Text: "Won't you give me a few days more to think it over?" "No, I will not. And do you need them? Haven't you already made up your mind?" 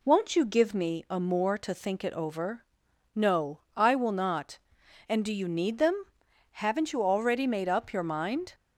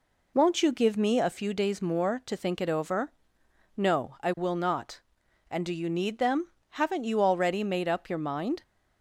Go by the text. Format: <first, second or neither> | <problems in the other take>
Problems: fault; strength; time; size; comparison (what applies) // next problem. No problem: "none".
second | skips "few days"; at 1.1 s